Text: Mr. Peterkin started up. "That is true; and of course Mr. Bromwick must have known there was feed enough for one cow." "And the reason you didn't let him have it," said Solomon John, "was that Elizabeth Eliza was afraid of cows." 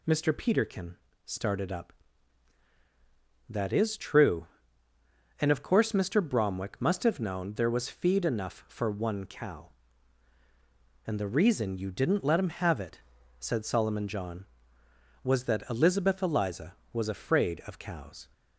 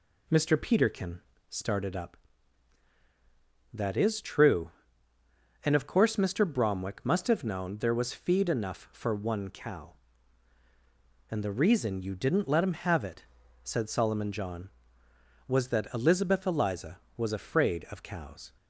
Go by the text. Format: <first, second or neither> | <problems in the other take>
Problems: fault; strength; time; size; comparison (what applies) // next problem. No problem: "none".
first | starts louder than the rest; slight; until 1.6 s; 2 dB // pauses between "Peterkin" and "started"; slight; at 1.2 s; 0.28 s long; slight in the first